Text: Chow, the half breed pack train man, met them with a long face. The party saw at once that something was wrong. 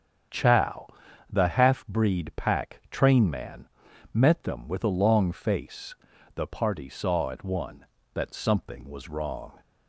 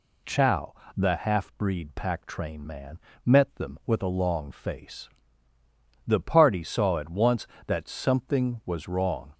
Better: second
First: starts louder than the rest; strong; until 1.7 s; 8 dB // says "one" for "once"; at 7.4 s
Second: none

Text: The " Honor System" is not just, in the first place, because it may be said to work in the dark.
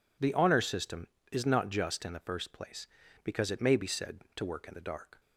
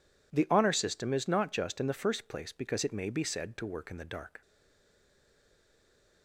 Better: first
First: none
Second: stays silent after the last word; noticeable; from 4.4 s on; 1.8 s long

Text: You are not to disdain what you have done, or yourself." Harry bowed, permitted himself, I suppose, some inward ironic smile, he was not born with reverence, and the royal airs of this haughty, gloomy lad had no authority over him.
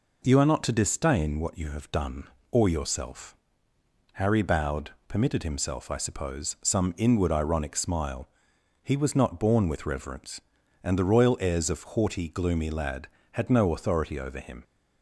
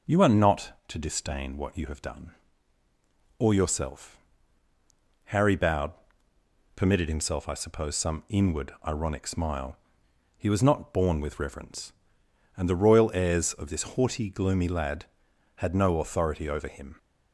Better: second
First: skips "this"; at 11.8 s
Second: none

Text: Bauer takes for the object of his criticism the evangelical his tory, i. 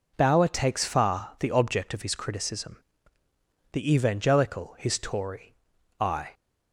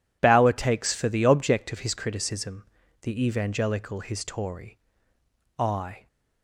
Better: second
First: says "far" for "for"; at 0.8 s // pauses between "criticism" and "the"; noticeable; at 2.7 s; 0.94 s long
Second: pauses between "criticism" and "the"; at 2.6 s; 0.38 s long

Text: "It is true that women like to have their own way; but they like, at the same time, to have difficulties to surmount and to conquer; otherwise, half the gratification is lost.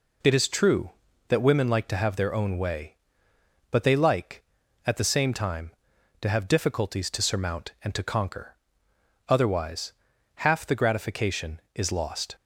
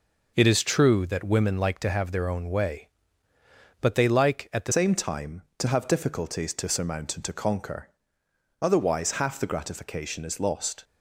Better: first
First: none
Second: changes voice at "same"; from 4.7 s on; 6.1 s long

